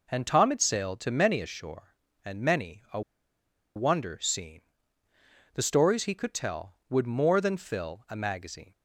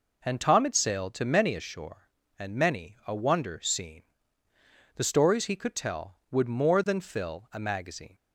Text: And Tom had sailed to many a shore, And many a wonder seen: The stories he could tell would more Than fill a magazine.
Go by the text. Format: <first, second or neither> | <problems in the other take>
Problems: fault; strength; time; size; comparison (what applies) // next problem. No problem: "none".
second | pauses between "a" and "wonder"; noticeable; at 3.0 s; 0.74 s long